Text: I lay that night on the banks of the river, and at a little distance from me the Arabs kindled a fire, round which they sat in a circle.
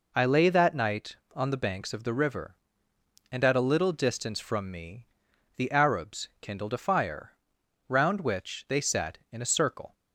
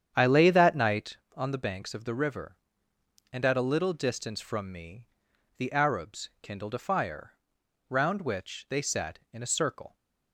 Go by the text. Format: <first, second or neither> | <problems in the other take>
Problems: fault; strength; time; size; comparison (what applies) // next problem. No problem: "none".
first | starts louder than the rest; strong; until 1.2 s; 8.5 dB // pauses between "me" and "the"; noticeable; at 5.0 s; 0.50 s long; noticeable in the first